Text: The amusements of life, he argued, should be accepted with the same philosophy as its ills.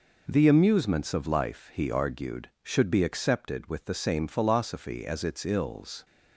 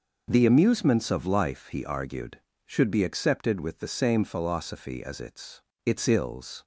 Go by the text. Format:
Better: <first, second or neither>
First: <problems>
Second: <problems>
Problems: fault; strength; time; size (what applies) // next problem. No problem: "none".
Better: first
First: none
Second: says "its" twice; at 5.8 s